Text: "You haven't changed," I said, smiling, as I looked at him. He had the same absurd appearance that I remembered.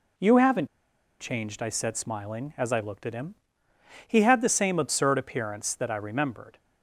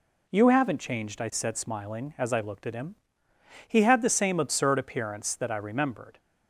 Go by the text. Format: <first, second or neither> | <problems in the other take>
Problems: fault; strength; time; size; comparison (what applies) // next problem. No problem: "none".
second | pauses between "haven't" and "changed"; noticeable; at 0.6 s; 0.55 s long